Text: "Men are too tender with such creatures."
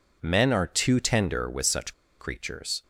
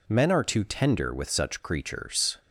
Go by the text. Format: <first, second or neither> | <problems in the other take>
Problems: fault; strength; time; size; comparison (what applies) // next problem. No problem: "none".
second | pauses between "such" and "creatures"; slight; at 1.9 s; 0.27 s long